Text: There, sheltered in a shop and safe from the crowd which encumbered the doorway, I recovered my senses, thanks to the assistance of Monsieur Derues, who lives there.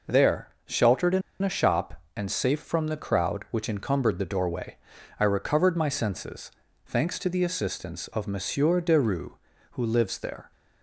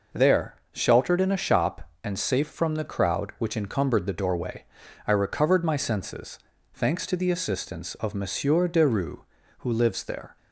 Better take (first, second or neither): second